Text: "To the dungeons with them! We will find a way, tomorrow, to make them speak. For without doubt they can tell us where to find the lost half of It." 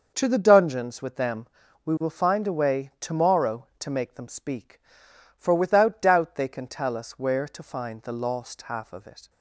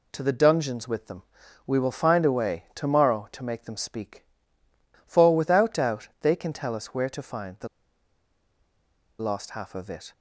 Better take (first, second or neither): first